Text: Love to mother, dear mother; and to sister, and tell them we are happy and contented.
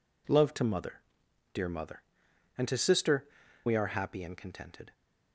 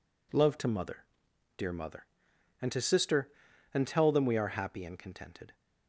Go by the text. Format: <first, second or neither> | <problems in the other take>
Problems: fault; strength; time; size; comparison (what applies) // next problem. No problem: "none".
second | skips "and tell them"; at 3.4 s